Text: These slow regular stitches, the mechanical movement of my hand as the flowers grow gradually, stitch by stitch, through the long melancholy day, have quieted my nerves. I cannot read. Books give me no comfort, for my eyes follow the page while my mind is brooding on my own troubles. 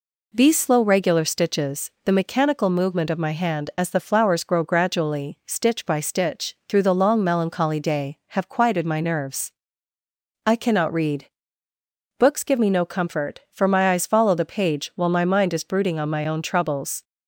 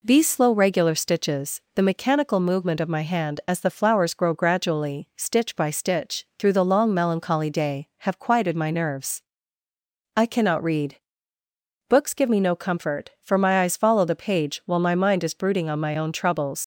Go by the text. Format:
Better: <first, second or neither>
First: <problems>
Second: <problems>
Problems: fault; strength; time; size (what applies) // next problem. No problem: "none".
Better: first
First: none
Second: leaves "troubles" unfinished; at 16.6 s; 95 ms